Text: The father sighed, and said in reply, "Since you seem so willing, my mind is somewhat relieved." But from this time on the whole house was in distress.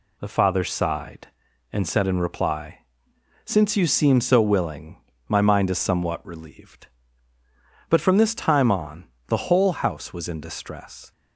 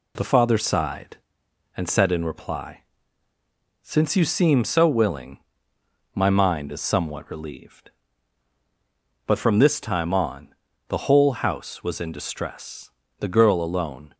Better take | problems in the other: first | pauses between "on" and "the"; slight; at 10.5 s; 0.34 s long; slight in the first // goes on to say "The girl alone"; noticeable; from 13.2 s on; 0.94 s long

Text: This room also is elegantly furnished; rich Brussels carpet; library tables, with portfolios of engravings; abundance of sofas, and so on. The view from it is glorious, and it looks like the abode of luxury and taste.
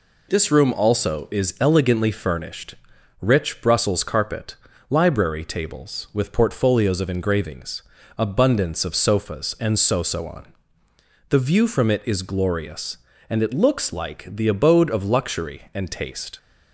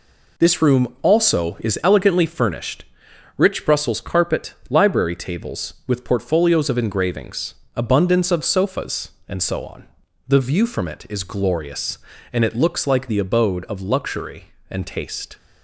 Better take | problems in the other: second | says "so" twice; at 10.0 s

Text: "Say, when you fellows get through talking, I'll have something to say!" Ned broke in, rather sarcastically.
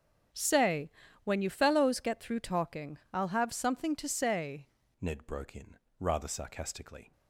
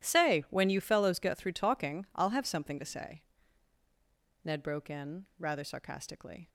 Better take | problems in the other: second | starts louder than the rest; strong; until 1.6 s; 8 dB // changes voice at "Ned"; from 4.9 s on; 2.2 s long

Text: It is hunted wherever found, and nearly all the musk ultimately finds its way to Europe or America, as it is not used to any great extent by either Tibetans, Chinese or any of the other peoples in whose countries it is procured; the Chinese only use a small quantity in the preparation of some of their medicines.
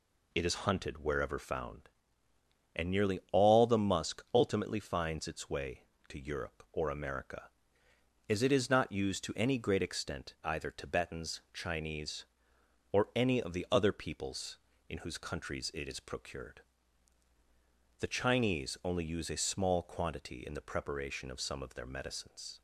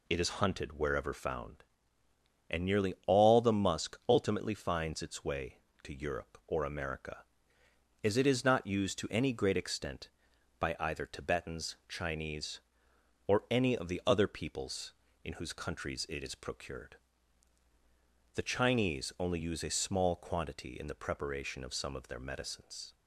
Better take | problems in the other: second | skips "by"; at 10.3 s

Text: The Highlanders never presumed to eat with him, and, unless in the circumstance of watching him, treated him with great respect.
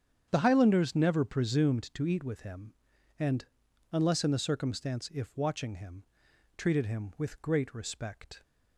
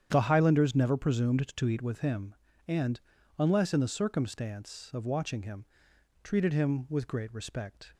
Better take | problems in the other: second | starts louder than the rest; strong; until 1.3 s; 8 dB; strong in the second // says "if" for "of"; at 5.1 s

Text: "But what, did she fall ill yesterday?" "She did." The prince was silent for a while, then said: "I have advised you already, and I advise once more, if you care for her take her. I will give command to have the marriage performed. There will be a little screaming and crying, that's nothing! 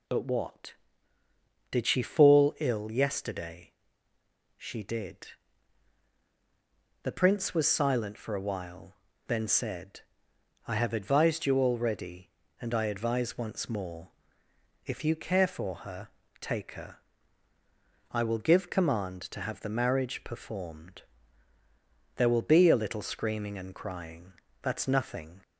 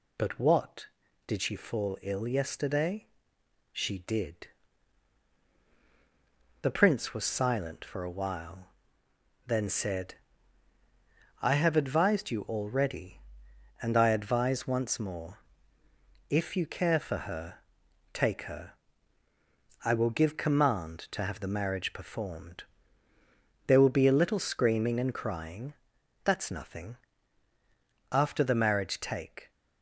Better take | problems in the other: first | pauses between "her" and "take"; noticeable; at 17.5 s; 0.54 s long; slight in the first // goes on to say "After the marriage take"; from 28.1 s on; 1.3 s long

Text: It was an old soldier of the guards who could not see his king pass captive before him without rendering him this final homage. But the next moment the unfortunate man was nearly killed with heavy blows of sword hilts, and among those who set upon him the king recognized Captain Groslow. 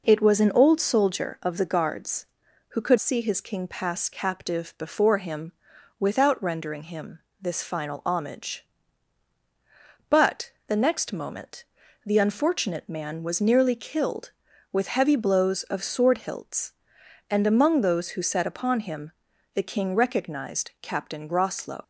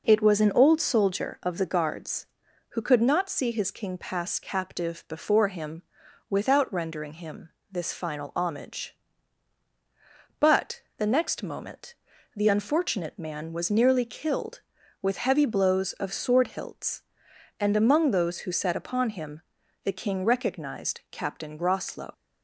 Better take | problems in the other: second | skips "not"; at 2.9 s // pauses between "him" and "without"; noticeable; at 5.5 s; 0.48 s long; noticeable in the second // pauses between "him" and "this"; slight; at 7.1 s; 0.22 s long; slight in the second // pauses between "But" and "the"; slight; at 10.5 s; 0.18 s long; slight in the second // pauses between "moment" and "the"; at 11.6 s; 0.40 s long; also in the second // pauses between "him" and "the"; at 19.1 s; 0.44 s long; also in the second

